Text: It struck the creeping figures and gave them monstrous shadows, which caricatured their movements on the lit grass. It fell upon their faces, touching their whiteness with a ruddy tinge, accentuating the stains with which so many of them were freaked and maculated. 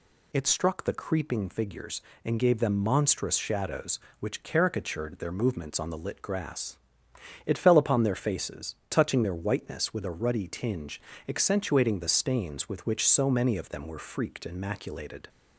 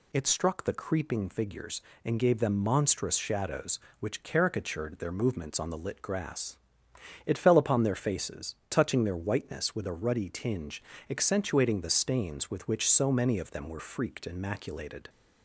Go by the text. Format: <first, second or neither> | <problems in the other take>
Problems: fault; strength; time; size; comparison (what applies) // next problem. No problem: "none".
neither | none